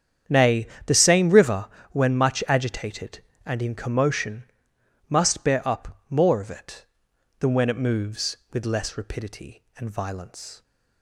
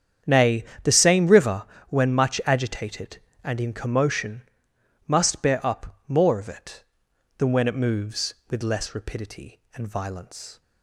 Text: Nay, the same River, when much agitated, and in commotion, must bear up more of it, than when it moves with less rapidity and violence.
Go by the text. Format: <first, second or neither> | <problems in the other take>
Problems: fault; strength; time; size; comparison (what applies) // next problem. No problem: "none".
neither | starts louder than the rest; strong; the same in both